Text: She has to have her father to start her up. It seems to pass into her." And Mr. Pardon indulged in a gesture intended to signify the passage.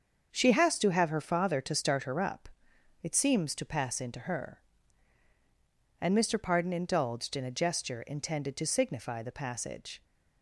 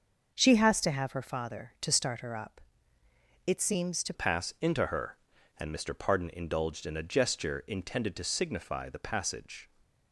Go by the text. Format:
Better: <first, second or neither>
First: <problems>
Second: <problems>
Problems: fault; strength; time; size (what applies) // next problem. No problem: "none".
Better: first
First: starts louder than the rest; until 1.3 s; 7 dB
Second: starts louder than the rest; until 1.3 s; 6 dB // changes voice at "pass"; from 4.1 s on; 5.5 s long